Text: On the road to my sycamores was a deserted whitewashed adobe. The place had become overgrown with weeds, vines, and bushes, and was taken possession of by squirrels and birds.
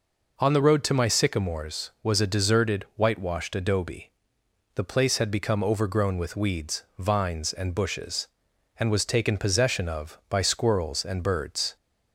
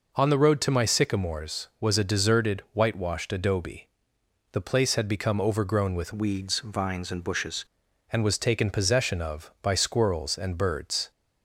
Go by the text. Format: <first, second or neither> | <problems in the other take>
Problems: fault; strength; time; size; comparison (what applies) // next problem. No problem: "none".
first | changes voice from "weeds" to "bushes"; from 6.1 to 7.6 s; 1.5 s long